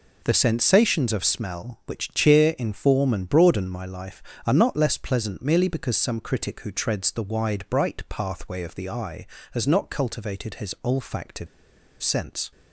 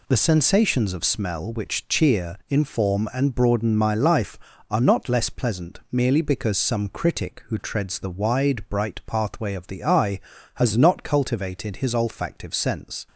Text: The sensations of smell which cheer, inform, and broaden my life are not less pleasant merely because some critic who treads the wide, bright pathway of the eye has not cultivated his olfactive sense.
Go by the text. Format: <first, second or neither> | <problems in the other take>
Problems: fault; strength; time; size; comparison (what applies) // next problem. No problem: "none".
second | pauses between "olfactive" and "sense"; noticeable; at 11.4 s; 0.55 s long